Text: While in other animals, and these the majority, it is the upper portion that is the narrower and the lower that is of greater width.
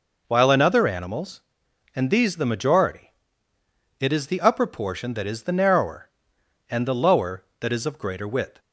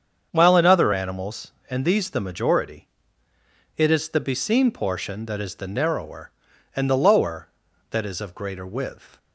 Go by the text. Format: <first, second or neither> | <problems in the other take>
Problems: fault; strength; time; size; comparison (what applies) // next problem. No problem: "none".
first | starts louder than the rest; strong; until 1.3 s; 7.5 dB // says "beseen" for "upper"; at 4.1 s